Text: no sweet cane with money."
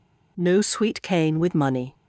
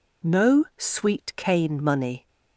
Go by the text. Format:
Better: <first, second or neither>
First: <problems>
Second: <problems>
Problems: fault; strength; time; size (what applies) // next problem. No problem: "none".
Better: first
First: none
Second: skips "with"; at 1.8 s